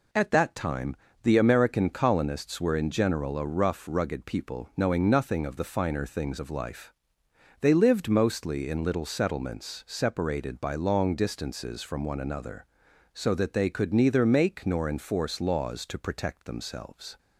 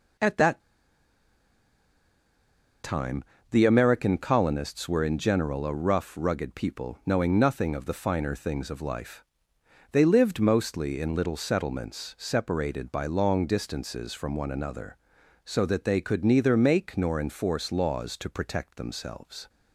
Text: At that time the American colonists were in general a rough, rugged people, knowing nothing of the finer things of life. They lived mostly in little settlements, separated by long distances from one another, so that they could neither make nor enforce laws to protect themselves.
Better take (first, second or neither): first